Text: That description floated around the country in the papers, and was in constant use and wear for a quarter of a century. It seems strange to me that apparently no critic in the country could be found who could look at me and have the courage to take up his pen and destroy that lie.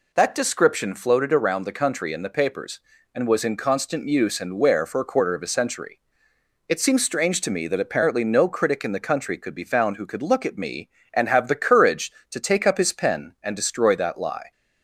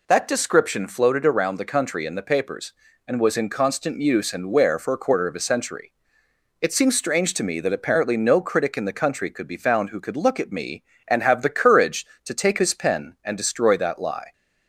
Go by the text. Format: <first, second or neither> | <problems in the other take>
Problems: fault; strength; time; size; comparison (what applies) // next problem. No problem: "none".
first | skips "up"; at 12.5 s